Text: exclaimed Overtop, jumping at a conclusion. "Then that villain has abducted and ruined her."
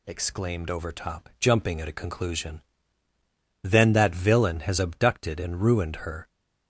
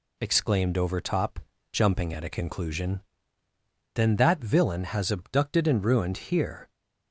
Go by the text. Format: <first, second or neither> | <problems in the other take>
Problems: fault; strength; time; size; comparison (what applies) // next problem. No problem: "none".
first | says "here" for "her"; at 6.1 s